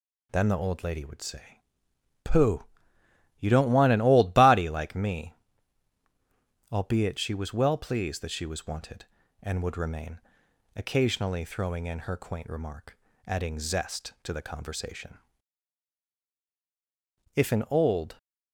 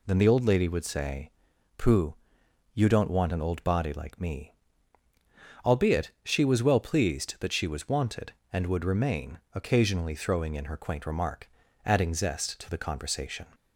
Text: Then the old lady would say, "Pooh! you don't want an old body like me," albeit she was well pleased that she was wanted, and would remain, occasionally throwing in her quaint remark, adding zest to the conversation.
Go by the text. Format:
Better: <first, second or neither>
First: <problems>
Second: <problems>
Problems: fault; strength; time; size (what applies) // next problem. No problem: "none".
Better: second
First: goes on to say "If an old"; noticeable; from 17.3 s on; 0.82 s long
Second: none